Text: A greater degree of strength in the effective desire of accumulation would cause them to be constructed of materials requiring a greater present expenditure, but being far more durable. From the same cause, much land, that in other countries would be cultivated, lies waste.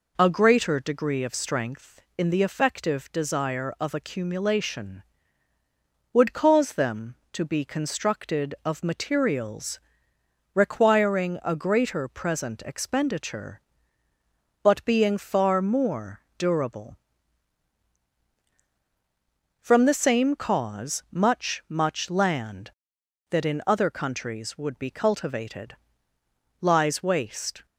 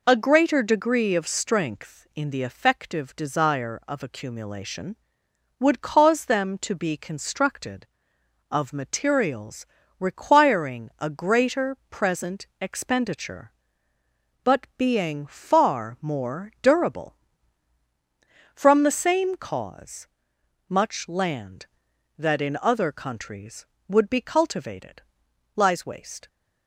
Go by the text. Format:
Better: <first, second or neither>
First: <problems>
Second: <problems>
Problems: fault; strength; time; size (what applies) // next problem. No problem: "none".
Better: second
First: pauses between "materials" and "requiring"; noticeable; at 9.7 s; 0.76 s long // pauses between "more" and "durable"; slight; at 16.2 s; 0.16 s long // says "much" twice; at 21.6 s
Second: pauses between "materials" and "requiring"; slight; at 9.6 s; 0.36 s long